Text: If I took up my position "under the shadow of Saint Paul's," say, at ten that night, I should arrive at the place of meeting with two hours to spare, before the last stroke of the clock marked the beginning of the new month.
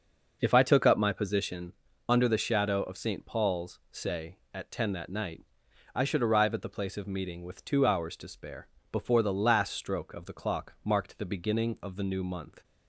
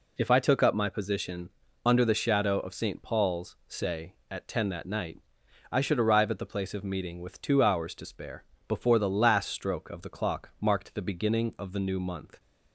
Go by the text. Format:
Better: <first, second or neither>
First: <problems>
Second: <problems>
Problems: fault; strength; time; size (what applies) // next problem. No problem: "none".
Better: second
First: starts louder than the rest; noticeable; until 1.5 s; 6 dB // pauses between "position" and "under"; slight; at 1.7 s; 0.34 s long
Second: pauses between "position" and "under"; slight; at 1.5 s; 0.34 s long